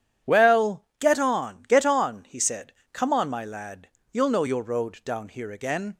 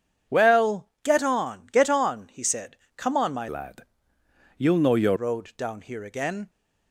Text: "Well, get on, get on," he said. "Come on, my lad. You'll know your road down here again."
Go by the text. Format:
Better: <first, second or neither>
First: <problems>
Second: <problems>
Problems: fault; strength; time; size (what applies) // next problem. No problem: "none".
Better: first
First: none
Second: starts louder than the rest; strong; until 1.4 s; 8 dB // changes voice from "lad" to "your"; from 3.4 to 5.1 s; 1.7 s long